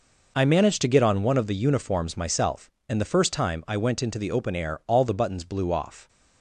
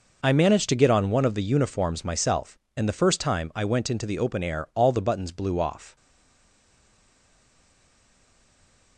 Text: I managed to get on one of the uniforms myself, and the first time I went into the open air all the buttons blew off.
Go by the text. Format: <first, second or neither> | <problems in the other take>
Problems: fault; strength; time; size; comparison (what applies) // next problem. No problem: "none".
first | stays silent after the last word; strong; from 5.9 s on; 3.0 s long